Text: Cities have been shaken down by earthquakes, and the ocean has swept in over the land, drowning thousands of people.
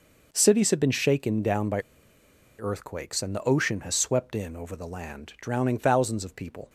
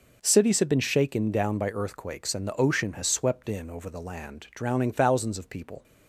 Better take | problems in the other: second | pauses between "by" and "earthquakes"; noticeable; at 1.8 s; 0.77 s long

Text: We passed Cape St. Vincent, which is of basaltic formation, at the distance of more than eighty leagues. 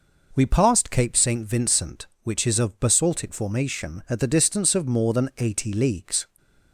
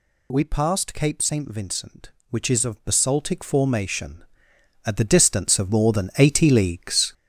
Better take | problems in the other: first | gets louder; strong; throughout; 8.5 dB

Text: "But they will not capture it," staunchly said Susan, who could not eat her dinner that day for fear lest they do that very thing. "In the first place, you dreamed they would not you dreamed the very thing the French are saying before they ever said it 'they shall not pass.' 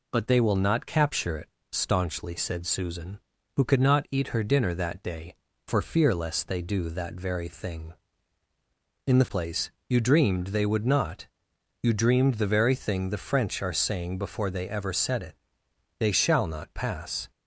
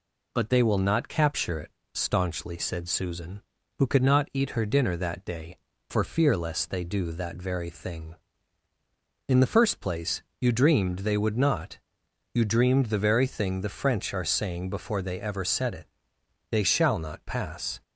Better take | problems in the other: second | skips "first"; at 9.2 s // pauses between "not" and "you"; noticeable; at 11.2 s; 0.54 s long; noticeable in the second // pauses between "it" and "they"; noticeable; at 15.3 s; 0.64 s long; noticeable in the second

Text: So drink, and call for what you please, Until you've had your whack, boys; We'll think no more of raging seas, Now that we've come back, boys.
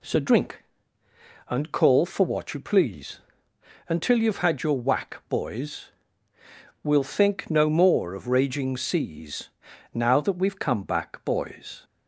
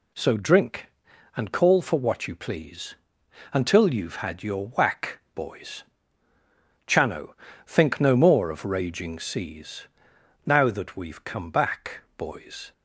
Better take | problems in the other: first | says "Chano" for "We'll"; at 6.8 s

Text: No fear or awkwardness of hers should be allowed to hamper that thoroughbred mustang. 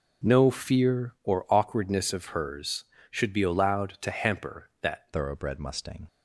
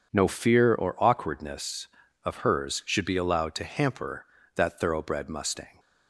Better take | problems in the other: second | changes voice at "thoroughbred"; from 5.1 s on; 0.9 s long

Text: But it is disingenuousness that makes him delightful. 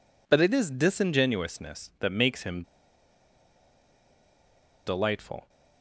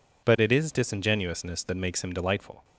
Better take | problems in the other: second | pauses between "him" and "delightful"; strong; at 2.6 s; 2.2 s long

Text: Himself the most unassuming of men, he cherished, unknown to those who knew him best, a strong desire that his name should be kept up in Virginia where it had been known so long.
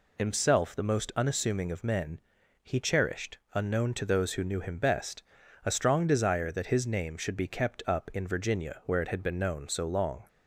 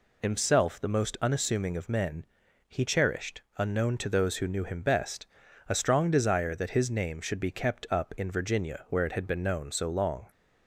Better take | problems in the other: neither | none

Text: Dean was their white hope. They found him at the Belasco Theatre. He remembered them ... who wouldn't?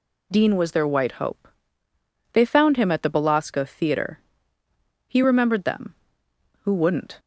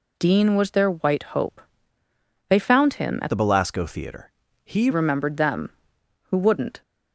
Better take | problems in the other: first | changes voice from "the" to "He"; from 3.2 to 4.8 s; 1.6 s long

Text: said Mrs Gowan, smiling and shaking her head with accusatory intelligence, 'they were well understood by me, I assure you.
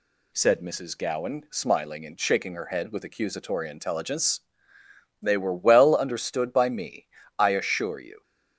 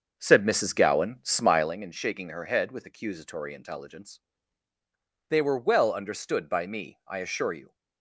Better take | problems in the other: first | starts louder than the rest; until 1.7 s; 6.5 dB

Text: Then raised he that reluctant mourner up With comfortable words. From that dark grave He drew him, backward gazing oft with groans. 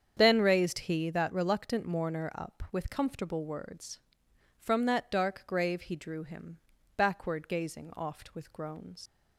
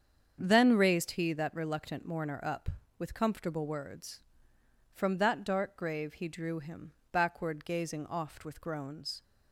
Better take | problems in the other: second | starts louder than the rest; strong; until 1.1 s; 7.5 dB; strong in the second // leaves "groans" unfinished; at 9.0 s; 70 ms

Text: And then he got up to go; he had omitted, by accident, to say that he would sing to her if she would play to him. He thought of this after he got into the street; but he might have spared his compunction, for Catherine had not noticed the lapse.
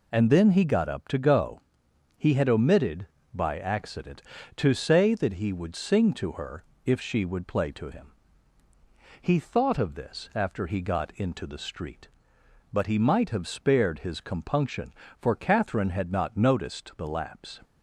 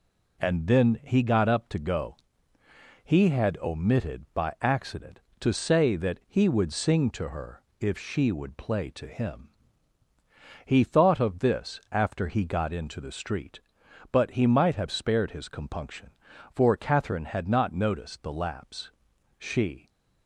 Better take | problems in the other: first | pauses between "her" and "if"; slight; at 7.6 s; 0.20 s long; slight in the first // goes on to say "She"; from 19.3 s on; 0.50 s long

